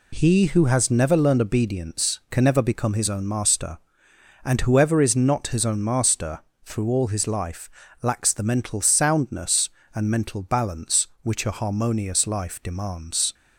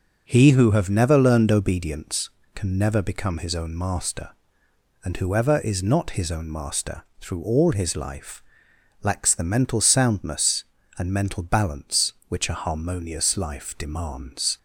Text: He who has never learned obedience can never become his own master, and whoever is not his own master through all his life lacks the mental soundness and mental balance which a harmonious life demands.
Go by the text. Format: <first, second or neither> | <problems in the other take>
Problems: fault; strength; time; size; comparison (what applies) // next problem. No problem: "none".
first | says "have" for "has"; at 0.7 s // pauses between "master" and "through"; slight; at 7.0 s; 0.16 s long; slight in the first // pauses between "life" and "lacks"; noticeable; at 8.4 s; 0.62 s long; slight in the first